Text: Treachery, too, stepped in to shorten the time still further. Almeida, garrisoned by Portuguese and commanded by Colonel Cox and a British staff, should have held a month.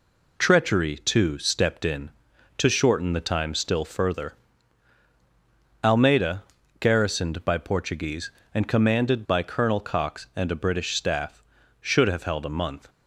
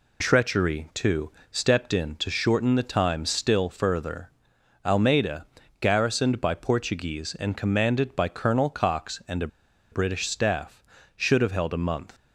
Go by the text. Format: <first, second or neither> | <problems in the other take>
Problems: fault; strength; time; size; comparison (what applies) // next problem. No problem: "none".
first | pauses between "a" and "British"; at 9.4 s; 0.44 s long